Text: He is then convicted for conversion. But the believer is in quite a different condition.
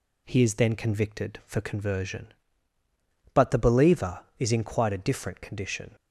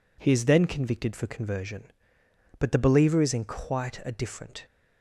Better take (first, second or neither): first